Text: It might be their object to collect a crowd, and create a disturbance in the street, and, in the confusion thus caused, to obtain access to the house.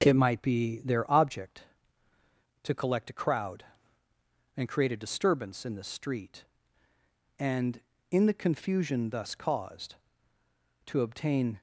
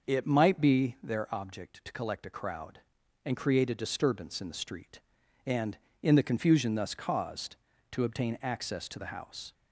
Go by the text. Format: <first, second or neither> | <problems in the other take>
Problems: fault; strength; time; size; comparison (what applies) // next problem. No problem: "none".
second | stops before "access to the house"; at 11.5 s